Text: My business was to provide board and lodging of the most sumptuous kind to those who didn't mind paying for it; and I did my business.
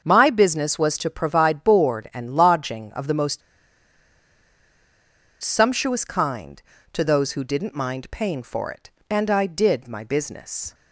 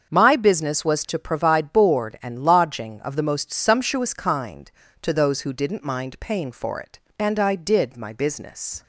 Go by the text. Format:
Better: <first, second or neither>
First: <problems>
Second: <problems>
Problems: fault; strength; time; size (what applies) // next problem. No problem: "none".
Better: second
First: starts louder than the rest; until 1.0 s; 7 dB // pauses between "most" and "sumptuous"; strong; at 3.4 s; 2.0 s long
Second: starts louder than the rest; until 1.1 s; 7 dB